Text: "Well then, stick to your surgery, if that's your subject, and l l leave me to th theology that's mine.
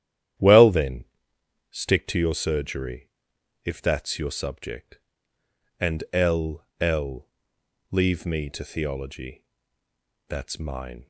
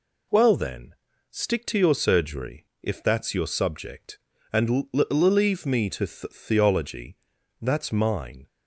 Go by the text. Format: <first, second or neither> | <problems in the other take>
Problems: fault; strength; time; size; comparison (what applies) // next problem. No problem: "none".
second | starts louder than the rest; strong; until 2.0 s; 11 dB // pauses between "l" and "l"; slight; at 6.6 s; 0.16 s long // pauses between "l" and "leave"; noticeable; at 7.2 s; 0.64 s long // skips "th"; at 8.6 s // pauses between "theology" and "that's"; noticeable; at 9.4 s; 0.86 s long; noticeable in the second